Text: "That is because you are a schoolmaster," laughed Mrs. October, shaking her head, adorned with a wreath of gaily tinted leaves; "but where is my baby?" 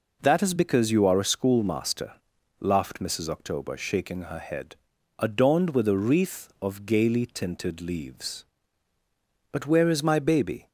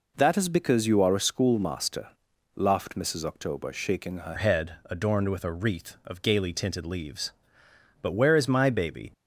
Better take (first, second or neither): first